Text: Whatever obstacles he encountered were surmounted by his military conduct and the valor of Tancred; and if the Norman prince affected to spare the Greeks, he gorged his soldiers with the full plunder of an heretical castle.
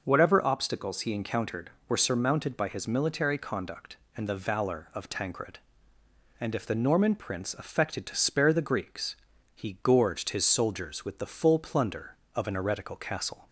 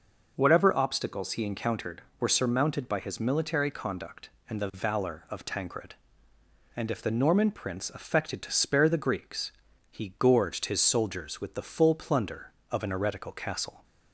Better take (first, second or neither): neither